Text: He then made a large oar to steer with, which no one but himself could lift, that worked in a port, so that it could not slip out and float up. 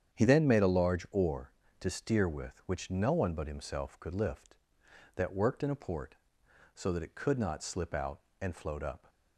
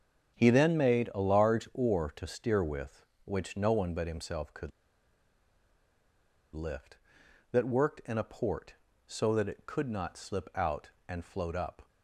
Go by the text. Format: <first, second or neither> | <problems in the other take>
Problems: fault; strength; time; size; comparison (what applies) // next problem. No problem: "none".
first | starts louder than the rest; strong; until 1.4 s; 8 dB; strong in the first // pauses between "could" and "lift"; strong; at 4.7 s; 1.8 s long